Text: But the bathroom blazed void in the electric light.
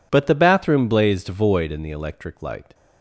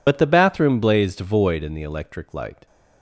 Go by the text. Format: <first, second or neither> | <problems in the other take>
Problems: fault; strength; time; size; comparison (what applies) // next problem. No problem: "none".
first | loses the start of "But"; at 0.0 s; 50 ms